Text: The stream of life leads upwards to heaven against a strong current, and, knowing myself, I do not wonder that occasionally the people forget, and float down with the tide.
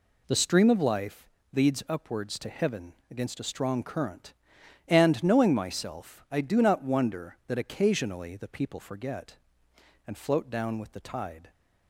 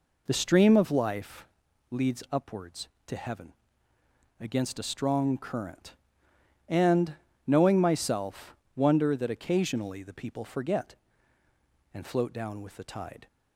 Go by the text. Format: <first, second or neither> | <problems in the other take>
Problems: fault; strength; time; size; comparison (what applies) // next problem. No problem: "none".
first | pauses between "life" and "leads"; at 1.4 s; 0.42 s long; slight in the first // pauses between "heaven" and "against"; noticeable; at 3.5 s; 0.88 s long; slight in the first // skips "I do not"; at 8.6 s